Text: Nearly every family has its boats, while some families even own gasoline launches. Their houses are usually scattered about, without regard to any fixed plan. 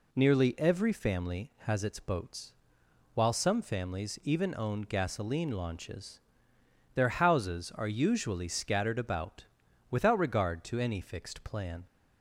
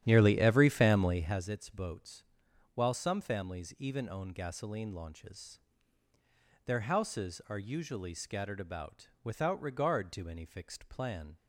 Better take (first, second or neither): first